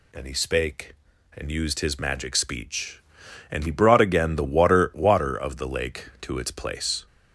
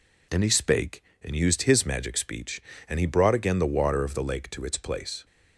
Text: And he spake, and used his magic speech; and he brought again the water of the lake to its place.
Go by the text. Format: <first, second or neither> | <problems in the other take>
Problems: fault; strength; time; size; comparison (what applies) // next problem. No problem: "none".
second | says "water" twice; at 4.9 s